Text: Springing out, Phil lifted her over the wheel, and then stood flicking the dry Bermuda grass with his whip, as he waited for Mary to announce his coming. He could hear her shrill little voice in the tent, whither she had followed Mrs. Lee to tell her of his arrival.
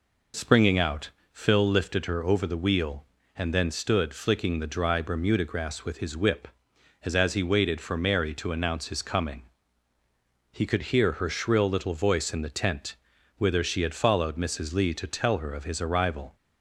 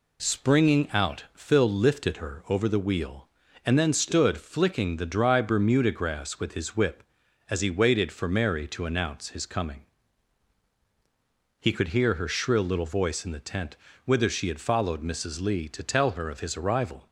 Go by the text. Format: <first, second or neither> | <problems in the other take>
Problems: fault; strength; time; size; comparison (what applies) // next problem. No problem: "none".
second | says "as" twice; at 7.1 s